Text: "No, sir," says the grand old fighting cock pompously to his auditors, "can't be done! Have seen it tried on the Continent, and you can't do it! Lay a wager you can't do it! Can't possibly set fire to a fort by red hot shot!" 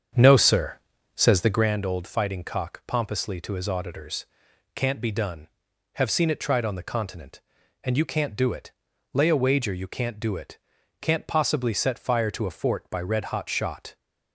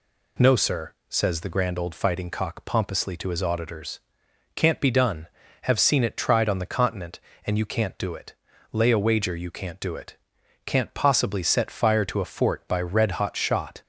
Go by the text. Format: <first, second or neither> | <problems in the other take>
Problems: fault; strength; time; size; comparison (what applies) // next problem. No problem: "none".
second | starts louder than the rest; strong; until 1.8 s; 7.5 dB